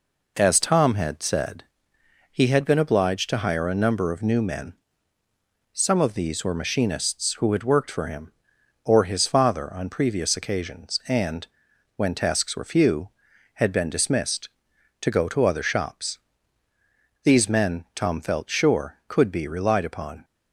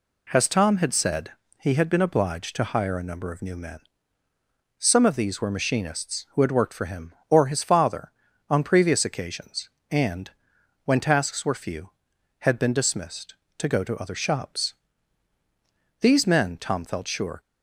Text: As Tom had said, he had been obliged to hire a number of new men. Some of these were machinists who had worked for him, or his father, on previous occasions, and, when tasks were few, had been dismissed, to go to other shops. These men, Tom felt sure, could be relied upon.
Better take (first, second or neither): first